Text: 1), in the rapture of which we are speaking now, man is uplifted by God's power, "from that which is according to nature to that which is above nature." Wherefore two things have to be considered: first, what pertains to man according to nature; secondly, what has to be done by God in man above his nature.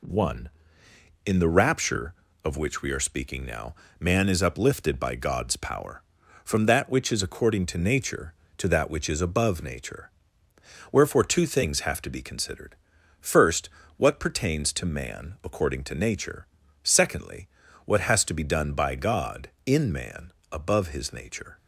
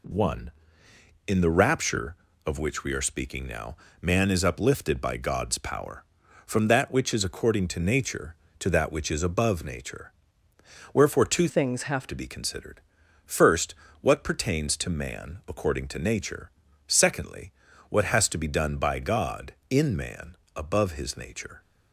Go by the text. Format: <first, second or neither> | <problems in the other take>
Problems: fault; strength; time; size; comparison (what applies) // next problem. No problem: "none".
first | changes voice from "things" to "have"; from 11.4 to 12.0 s; 0.6 s long // pauses between "man" and "above"; slight; at 20.3 s; 0.20 s long; slight in the first